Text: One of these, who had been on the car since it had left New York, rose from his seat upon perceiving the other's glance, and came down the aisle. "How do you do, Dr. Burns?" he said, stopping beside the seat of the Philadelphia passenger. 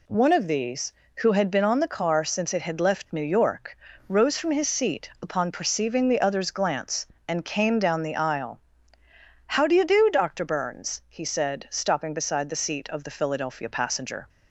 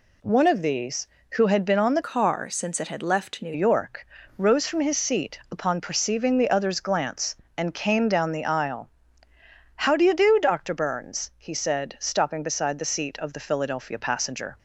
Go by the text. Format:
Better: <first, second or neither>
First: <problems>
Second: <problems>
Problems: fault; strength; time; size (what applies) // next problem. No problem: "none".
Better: first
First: none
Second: changes voice from "car" to "New"; from 2.0 to 3.5 s; 1.5 s long